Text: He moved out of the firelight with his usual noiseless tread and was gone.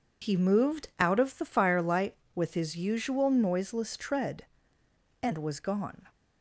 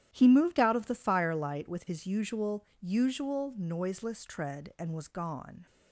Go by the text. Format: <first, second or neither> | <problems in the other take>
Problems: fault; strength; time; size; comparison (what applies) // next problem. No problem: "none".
first | starts louder than the rest; strong; until 1.1 s; 11.5 dB // says "usual" twice; at 2.7 s